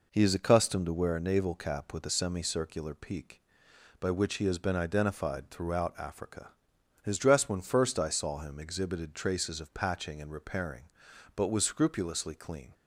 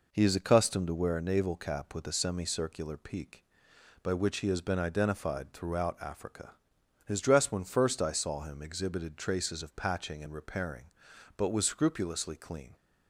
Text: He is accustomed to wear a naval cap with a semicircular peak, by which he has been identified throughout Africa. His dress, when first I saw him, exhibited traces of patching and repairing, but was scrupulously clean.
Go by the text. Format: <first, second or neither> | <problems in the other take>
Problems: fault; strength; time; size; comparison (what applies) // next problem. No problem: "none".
neither | none